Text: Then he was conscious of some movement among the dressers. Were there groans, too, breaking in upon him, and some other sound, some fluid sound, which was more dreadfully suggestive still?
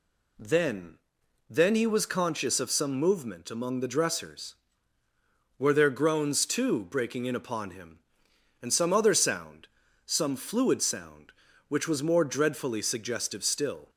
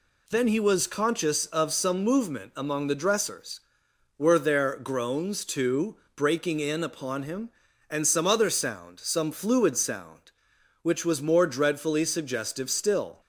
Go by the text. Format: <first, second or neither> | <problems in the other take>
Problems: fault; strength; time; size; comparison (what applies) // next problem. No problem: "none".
second | says "Then" twice; at 1.4 s